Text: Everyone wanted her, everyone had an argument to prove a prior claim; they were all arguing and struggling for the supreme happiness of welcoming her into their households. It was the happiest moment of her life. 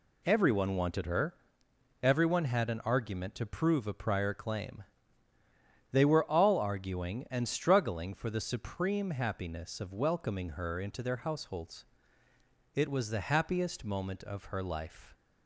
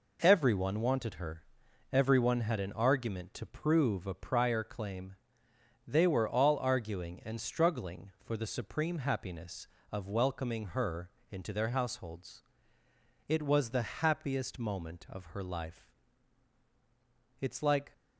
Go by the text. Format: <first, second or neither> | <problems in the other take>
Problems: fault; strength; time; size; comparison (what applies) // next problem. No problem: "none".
first | pauses between "her" and "into"; slight; at 11.0 s; 0.22 s long // goes on to say "It's like"; from 17.4 s on; 0.52 s long